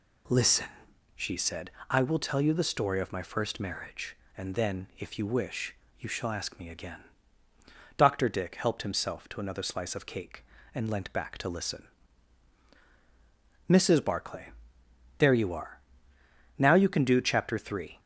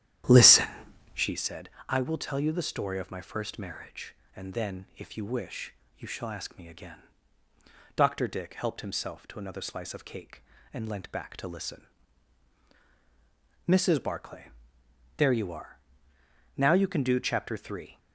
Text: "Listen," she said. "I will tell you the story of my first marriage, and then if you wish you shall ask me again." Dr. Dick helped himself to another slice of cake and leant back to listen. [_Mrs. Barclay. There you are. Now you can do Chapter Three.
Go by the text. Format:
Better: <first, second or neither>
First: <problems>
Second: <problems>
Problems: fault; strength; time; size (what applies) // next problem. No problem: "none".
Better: first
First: pauses between "wish" and "you"; slight; at 5.7 s; 0.24 s long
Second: starts louder than the rest; strong; until 1.4 s; 11 dB // pauses between "wish" and "you"; slight; at 5.7 s; 0.24 s long